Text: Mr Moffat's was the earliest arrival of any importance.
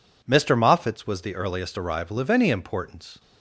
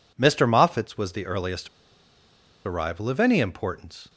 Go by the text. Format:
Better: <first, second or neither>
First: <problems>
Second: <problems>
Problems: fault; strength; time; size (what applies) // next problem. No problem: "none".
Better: first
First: none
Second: pauses between "earliest" and "arrival"; at 1.6 s; 0.99 s long